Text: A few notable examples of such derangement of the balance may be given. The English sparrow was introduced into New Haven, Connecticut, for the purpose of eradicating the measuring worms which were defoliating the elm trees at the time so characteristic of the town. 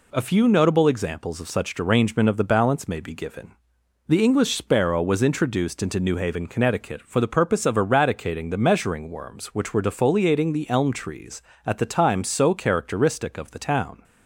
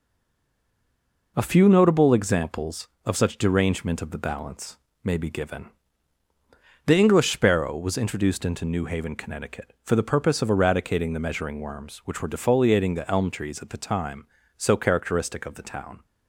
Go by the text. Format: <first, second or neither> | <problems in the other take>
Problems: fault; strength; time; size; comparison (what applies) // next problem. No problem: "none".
first | stays silent before the first word; noticeable; until 1.3 s; 1.3 s long // pauses between "balance" and "may"; slight; at 4.7 s; 0.26 s long